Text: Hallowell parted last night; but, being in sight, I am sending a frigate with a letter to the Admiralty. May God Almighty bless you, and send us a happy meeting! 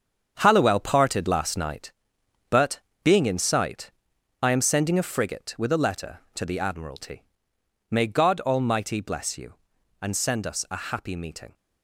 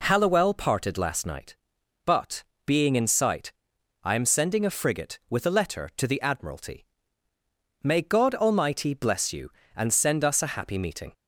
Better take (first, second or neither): second